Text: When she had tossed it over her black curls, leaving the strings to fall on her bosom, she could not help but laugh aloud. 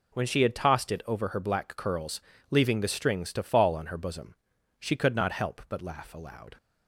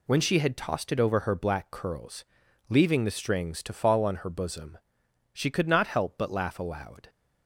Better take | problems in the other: neither | none

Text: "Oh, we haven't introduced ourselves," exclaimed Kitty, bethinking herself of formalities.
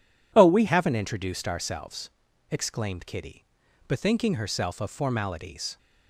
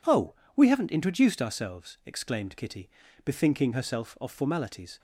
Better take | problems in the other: second | changes voice at "haven't"; from 0.6 s on; 5.1 s long

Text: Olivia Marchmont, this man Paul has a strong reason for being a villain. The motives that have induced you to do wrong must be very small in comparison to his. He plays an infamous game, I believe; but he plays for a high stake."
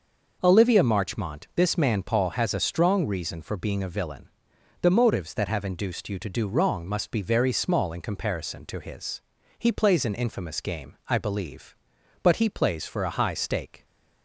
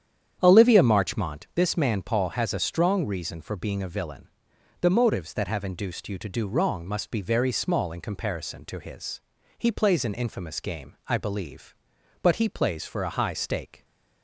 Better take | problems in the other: first | starts louder than the rest; strong; until 1.5 s; 9 dB

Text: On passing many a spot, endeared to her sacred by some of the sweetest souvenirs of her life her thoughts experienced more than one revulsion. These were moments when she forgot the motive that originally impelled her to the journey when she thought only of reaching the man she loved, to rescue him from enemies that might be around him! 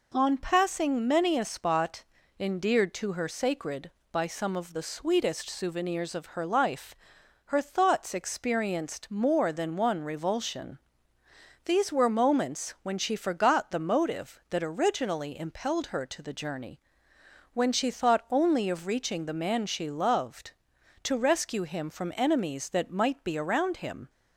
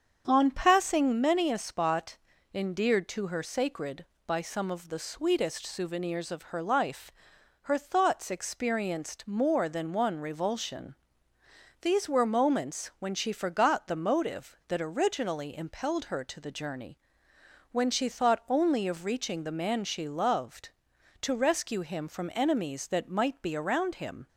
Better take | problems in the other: first | starts louder than the rest; strong; until 1.3 s; 7.5 dB // pauses between "life" and "her"; noticeable; at 7.1 s; 0.50 s long; noticeable in the first // pauses between "journey" and "when"; noticeable; at 16.9 s; 0.74 s long; noticeable in the first

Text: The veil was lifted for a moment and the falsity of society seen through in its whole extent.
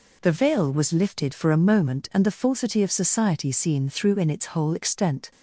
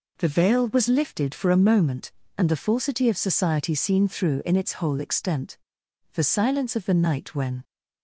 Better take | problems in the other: first | goes on to say "The silence of the night when"; from 6.1 s on; 1.5 s long

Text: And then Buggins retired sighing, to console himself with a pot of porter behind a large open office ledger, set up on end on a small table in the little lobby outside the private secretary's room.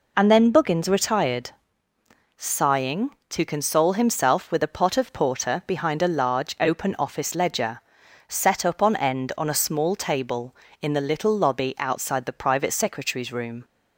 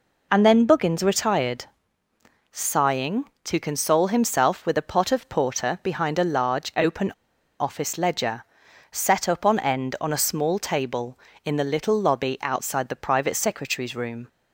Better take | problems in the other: first | pauses between "retired" and "sighing"; noticeable; at 1.6 s; 0.86 s long; noticeable in the first // pauses between "open" and "office"; noticeable; at 7.1 s; 0.49 s long

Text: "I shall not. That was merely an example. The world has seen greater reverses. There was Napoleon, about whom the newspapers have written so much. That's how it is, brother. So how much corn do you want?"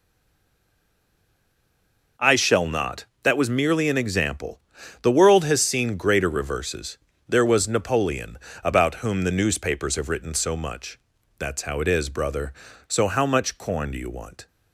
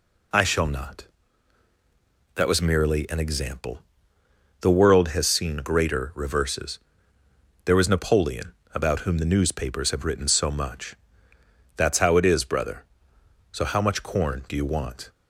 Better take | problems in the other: second | stays silent before the first word; until 2.1 s; 2.1 s long

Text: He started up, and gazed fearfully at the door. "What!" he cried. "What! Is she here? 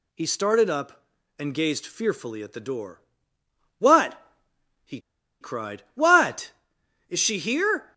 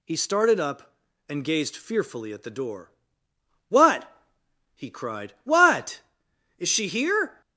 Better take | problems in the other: second | pauses between "he" and "cried"; at 4.9 s; 0.41 s long

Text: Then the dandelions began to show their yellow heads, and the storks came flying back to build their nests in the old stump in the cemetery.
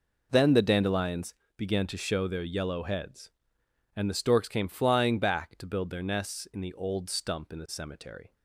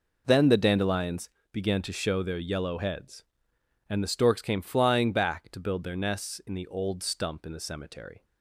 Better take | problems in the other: neither | pauses between "dandelions" and "began"; slight; the same in both

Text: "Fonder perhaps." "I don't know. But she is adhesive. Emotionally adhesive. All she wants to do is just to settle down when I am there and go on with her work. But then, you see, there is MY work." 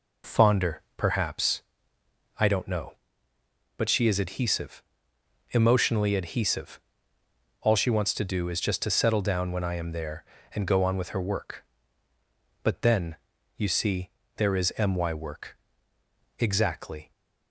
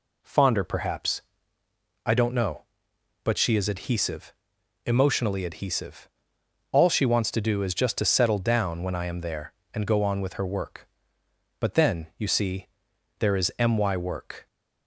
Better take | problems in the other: second | pauses between "Fonder" and "perhaps"; slight; at 0.8 s; 0.16 s long // goes on to say "Exactly"; noticeable; from 16.3 s on; 0.72 s long

